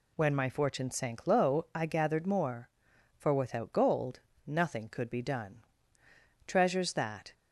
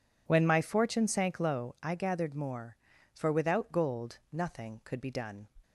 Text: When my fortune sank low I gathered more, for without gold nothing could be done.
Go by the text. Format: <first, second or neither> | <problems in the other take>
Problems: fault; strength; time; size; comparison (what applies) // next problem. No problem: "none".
second | pauses between "gold" and "nothing"; slight; at 4.1 s; 0.26 s long // goes on to say "Treasures that"; noticeable; from 6.4 s on; 0.88 s long